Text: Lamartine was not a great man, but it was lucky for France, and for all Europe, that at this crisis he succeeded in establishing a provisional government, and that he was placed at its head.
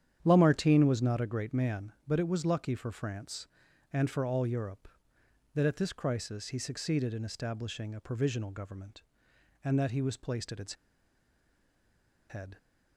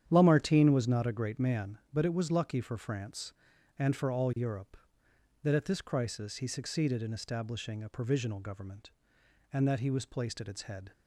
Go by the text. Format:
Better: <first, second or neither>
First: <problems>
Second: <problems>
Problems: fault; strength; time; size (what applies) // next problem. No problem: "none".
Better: second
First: starts louder than the rest; strong; until 1.2 s; 9.5 dB // pauses between "its" and "head"; strong; at 10.7 s; 1.5 s long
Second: starts louder than the rest; strong; until 1.0 s; 9.5 dB